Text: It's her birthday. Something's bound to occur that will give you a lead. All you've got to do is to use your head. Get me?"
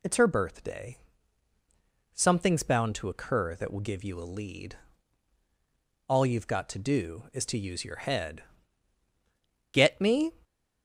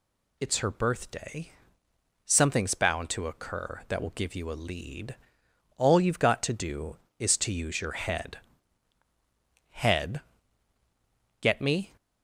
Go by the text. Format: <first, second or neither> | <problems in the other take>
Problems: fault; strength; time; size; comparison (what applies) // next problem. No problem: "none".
first | says "head" twice; at 9.6 s